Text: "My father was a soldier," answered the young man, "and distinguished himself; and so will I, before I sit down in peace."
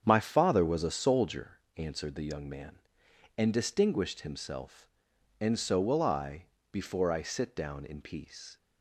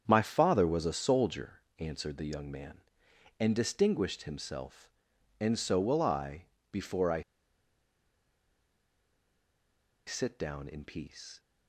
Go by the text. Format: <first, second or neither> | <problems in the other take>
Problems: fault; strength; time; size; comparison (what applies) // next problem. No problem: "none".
first | starts louder than the rest; strong; until 1.0 s; 8 dB; strong in the first // pauses between "I" and "sit"; strong; at 7.2 s; 2.8 s long